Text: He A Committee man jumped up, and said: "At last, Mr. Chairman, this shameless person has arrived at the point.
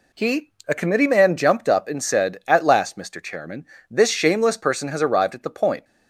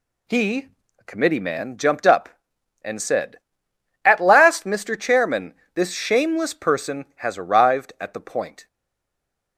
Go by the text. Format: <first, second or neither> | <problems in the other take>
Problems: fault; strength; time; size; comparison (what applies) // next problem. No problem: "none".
first | pauses between "He" and "A"; slight; at 0.6 s; 0.32 s long; slight in the first // stays silent after the last word; slight; from 8.6 s on; 0.9 s long